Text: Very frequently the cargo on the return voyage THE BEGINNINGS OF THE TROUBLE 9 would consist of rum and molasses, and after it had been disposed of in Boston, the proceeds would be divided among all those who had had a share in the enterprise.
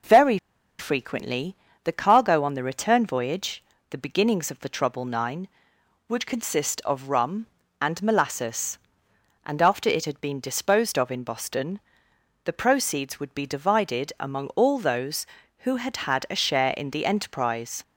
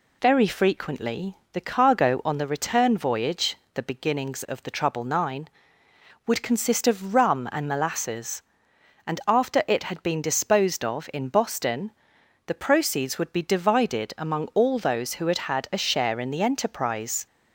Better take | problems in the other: second | pauses between "Very" and "frequently"; at 0.3 s; 0.42 s long // pauses between "frequently" and "the"; slight; at 1.5 s; 0.28 s long; slight in the second // pauses between "voyage" and "THE"; slight; at 3.6 s; 0.24 s long; slight in the second

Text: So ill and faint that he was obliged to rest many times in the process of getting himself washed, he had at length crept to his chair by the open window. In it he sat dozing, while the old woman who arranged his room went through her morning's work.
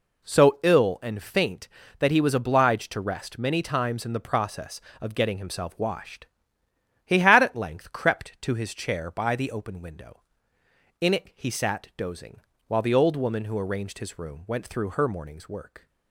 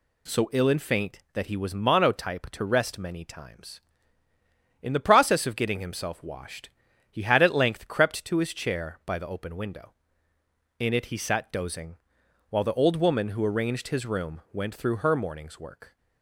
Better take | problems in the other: first | says "monotype" for "obliged"; at 1.7 s

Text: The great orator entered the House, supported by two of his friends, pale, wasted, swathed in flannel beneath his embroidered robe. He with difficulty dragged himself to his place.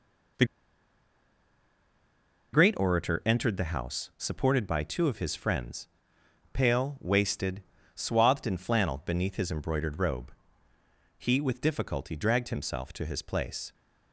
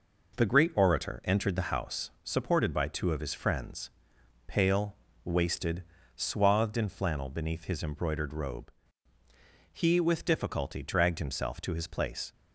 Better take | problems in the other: second | pauses between "The" and "great"; strong; at 0.4 s; 2.0 s long

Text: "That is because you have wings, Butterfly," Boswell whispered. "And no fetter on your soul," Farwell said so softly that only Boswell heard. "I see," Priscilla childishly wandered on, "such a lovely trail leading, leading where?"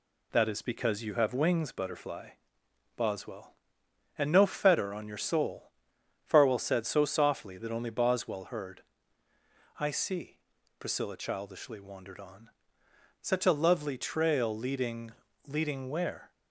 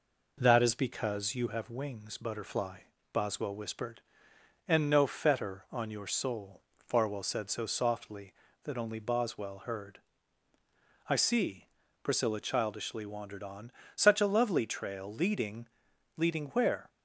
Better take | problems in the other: second | skips "whispered"; at 3.8 s

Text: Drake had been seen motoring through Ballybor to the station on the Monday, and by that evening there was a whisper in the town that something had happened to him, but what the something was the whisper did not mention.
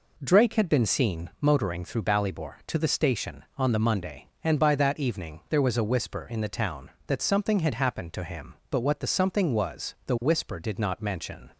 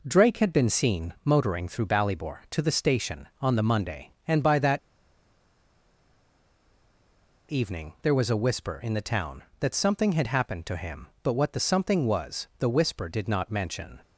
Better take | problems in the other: first | pauses between "that" and "evening"; strong; at 4.7 s; 2.7 s long

